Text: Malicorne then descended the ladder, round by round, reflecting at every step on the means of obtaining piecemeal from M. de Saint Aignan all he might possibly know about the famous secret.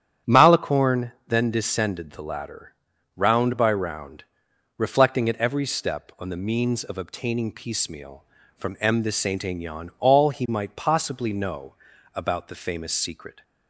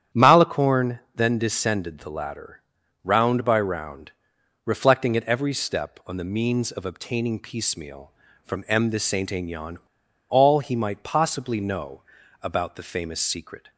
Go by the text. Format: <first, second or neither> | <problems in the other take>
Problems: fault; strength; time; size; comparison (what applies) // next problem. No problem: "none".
first | starts louder than the rest; strong; until 1.3 s; 9.5 dB; strong in the first // pauses between "Malicorne" and "then"; slight; at 0.9 s; 0.16 s long; slight in the first // pauses between "Aignan" and "all"; noticeable; at 9.7 s; 0.52 s long // pauses between "know" and "about"; at 12.0 s; 0.42 s long; also in the first